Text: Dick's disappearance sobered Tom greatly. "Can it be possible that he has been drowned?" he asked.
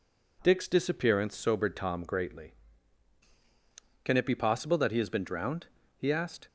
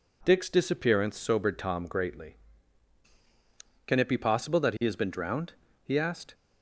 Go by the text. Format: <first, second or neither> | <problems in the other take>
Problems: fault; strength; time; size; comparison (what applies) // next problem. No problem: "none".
neither | none